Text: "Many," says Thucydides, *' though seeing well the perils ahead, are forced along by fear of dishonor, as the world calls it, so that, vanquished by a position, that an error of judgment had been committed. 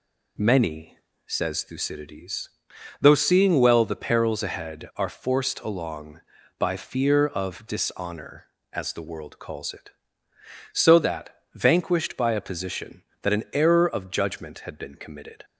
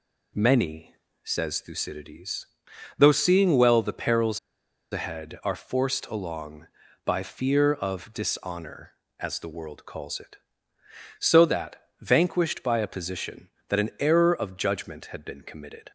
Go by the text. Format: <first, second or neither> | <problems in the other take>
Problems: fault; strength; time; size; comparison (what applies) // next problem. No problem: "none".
first | pauses between "perils" and "ahead"; noticeable; at 4.3 s; 0.53 s long